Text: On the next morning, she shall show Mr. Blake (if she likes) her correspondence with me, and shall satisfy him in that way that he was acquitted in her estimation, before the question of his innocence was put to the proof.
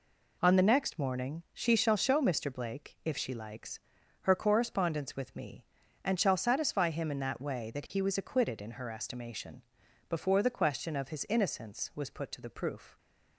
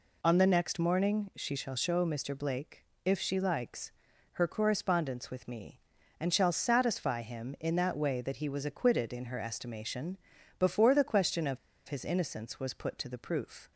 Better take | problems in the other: first | pauses between "of" and "his"; slight; at 11.5 s; 0.29 s long

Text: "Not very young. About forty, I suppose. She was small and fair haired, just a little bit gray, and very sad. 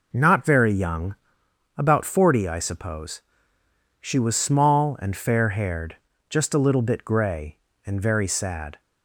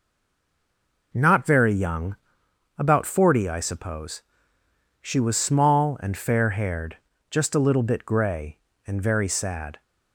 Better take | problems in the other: first | stays silent before the first word; until 1.1 s; 1.1 s long

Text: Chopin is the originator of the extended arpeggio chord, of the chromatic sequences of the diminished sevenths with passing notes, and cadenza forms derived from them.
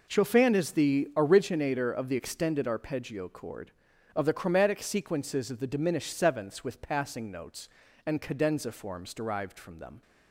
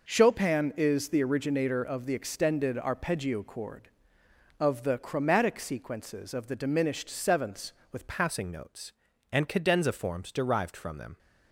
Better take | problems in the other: first | changes voice at "passing"; from 8.0 s on; 3.1 s long

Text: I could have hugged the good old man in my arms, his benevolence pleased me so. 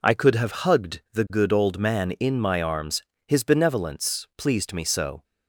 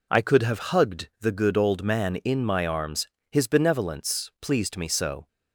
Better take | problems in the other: neither | none

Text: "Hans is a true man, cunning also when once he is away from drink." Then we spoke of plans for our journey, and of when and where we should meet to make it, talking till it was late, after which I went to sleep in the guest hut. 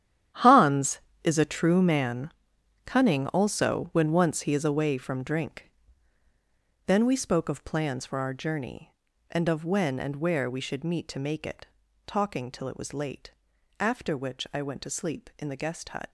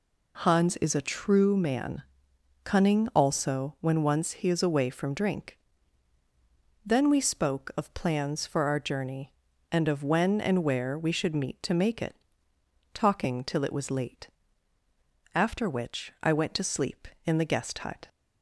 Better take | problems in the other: second | gets quieter; strong; throughout; 13 dB

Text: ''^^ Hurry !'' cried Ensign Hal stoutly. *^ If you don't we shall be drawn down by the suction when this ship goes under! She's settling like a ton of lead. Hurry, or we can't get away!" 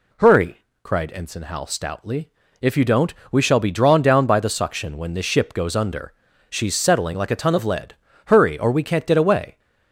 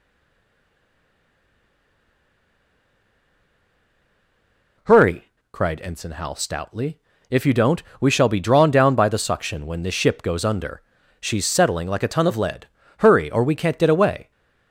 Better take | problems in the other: first | stays silent before the first word; strong; until 4.7 s; 4.7 s long // pauses between "don't" and "we"; slight; at 7.8 s; 0.18 s long; slight in the first

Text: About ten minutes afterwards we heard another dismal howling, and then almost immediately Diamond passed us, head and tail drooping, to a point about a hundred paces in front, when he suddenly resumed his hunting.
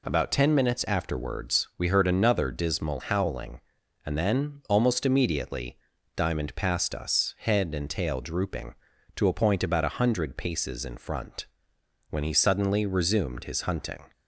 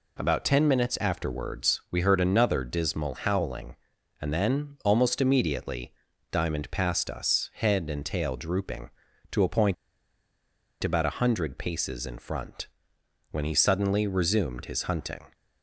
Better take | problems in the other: first | pauses between "immediately" and "Diamond"; at 5.9 s; 0.38 s long; also in the first // pauses between "point" and "about"; at 9.7 s; 1.0 s long

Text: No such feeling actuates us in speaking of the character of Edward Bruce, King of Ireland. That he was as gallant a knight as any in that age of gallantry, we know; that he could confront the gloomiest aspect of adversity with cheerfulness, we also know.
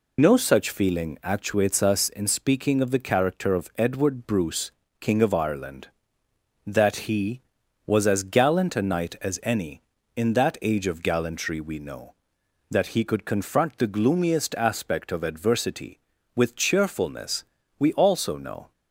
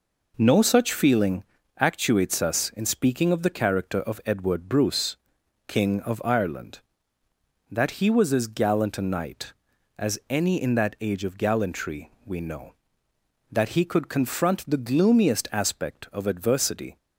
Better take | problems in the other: first | pauses between "feeling" and "actuates"; slight; at 1.4 s; 0.34 s long // stops before "with cheerfulness we also know"; at 16.9 s

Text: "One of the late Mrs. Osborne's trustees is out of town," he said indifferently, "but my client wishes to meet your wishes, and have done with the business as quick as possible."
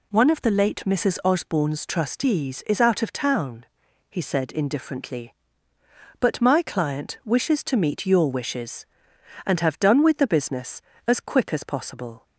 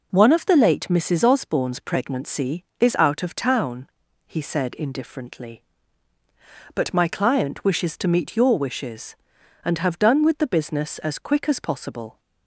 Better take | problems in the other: first | says "pregnancy" for "trustees"; at 1.7 s

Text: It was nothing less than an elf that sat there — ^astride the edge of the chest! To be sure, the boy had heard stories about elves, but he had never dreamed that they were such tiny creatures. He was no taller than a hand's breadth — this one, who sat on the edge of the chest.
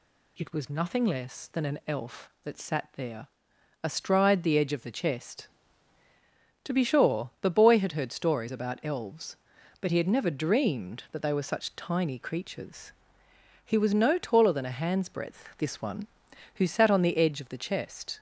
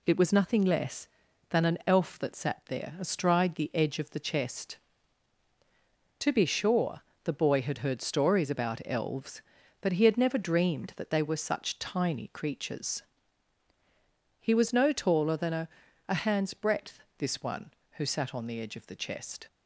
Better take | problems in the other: first | says "a" twice; at 16.0 s

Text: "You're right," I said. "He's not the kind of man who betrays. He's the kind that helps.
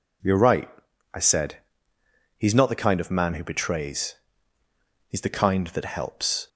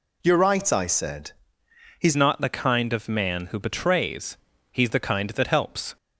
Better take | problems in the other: first | changes voice at "not"; from 2.1 s on; 3.8 s long

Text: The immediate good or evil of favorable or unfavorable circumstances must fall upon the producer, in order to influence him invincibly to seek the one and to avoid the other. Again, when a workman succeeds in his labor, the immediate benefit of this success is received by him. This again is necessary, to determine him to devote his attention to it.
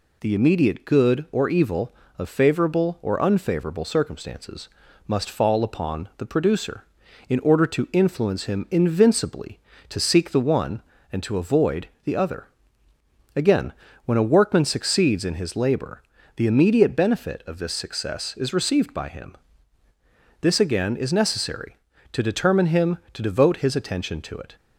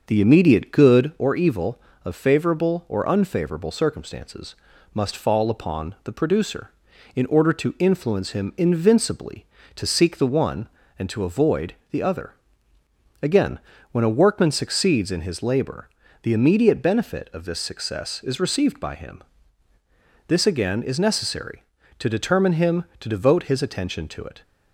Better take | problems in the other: first | starts louder than the rest; until 1.3 s; 6 dB // pauses between "circumstances" and "must"; at 4.5 s; 0.40 s long; also in the first // pauses between "avoid" and "the"; slight; at 11.7 s; 0.16 s long; slight in the first

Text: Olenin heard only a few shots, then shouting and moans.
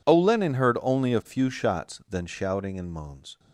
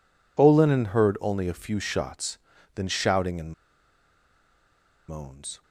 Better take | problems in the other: first | pauses between "and" and "moans"; strong; at 3.5 s; 1.5 s long

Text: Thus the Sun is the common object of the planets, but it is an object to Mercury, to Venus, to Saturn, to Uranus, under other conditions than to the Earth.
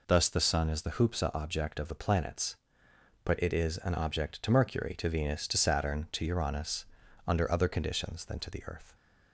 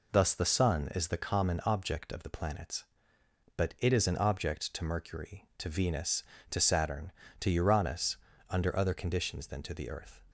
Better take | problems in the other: second | says "hoopsa" for "common"; at 0.9 s

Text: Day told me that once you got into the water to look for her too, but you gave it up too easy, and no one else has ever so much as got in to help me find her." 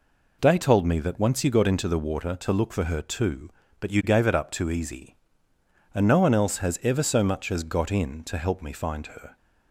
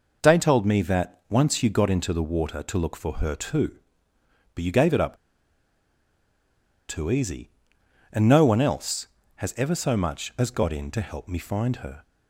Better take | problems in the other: first | pauses between "up" and "too"; strong; at 5.1 s; 1.7 s long

